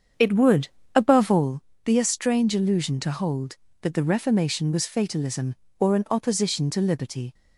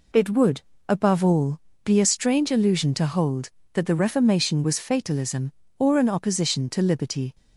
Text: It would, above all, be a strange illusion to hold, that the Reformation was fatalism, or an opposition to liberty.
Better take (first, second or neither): second